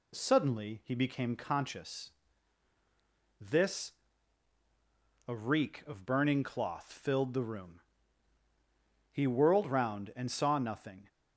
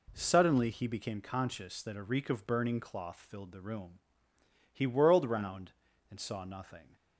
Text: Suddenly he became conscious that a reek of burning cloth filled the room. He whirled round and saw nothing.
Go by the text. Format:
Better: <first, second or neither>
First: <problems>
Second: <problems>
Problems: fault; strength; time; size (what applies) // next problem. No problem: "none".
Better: second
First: says "this" for "that"; at 3.3 s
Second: none